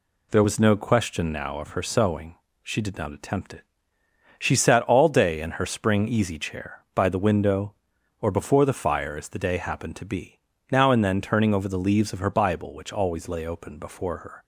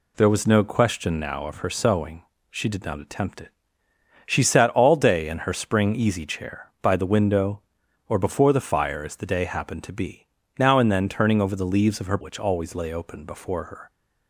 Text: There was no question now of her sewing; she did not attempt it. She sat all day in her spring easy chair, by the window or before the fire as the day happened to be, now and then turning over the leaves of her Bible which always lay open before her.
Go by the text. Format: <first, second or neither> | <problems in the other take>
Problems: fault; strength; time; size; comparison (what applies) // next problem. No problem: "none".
first | skips "Bible"; at 12.1 s